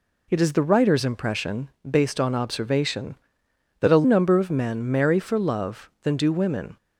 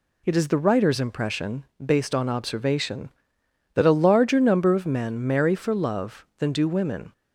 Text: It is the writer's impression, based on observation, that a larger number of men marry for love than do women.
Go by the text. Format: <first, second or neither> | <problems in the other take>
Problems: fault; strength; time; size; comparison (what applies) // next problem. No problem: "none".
second | skips "larger"; at 4.0 s